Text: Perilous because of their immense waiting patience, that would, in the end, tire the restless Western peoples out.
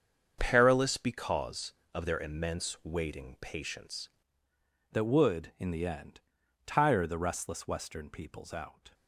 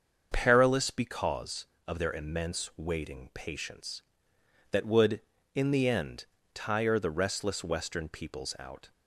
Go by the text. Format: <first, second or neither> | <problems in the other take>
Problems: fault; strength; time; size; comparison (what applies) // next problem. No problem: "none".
second | starts louder than the rest; until 1.4 s; 7 dB; also in the second // changes voice at "that"; from 4.9 s on; 4.0 s long